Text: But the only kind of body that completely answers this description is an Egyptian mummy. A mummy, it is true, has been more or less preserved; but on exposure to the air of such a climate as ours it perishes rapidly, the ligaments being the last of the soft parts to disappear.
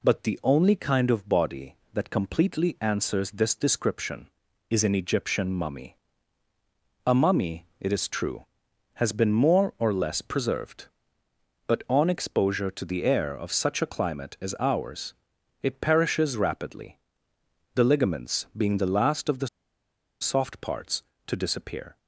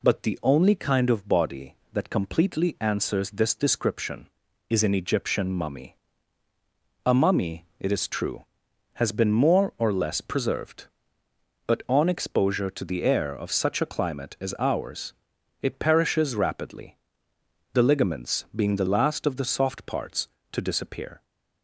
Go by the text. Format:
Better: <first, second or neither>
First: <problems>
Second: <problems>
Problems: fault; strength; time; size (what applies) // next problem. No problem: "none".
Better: second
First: pauses between "ours" and "it"; noticeable; at 15.1 s; 0.48 s long // pauses between "the" and "soft"; noticeable; at 19.4 s; 0.73 s long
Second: pauses between "ours" and "it"; noticeable; at 15.1 s; 0.48 s long